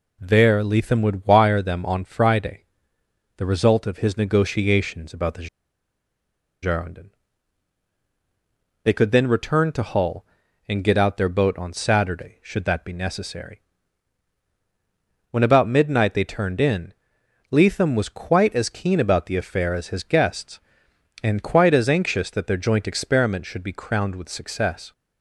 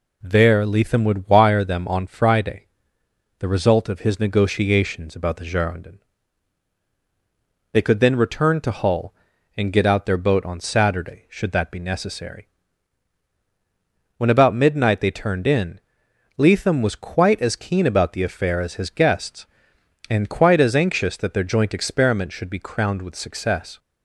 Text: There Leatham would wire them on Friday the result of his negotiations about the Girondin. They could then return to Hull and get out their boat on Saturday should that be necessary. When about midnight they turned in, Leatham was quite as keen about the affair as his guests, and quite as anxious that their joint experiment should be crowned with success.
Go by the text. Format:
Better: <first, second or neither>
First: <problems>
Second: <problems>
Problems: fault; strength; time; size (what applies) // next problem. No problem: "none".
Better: second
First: pauses between "Friday" and "the"; noticeable; at 2.6 s; 0.72 s long // pauses between "the" and "Girondin"; at 5.4 s; 1.1 s long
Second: pauses between "Friday" and "the"; noticeable; at 2.6 s; 0.72 s long